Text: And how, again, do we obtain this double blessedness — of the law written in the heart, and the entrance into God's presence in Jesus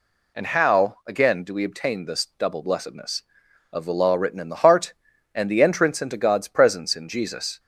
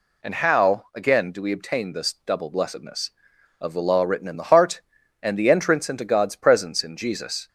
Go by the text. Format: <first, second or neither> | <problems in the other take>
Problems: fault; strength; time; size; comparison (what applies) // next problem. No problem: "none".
neither | none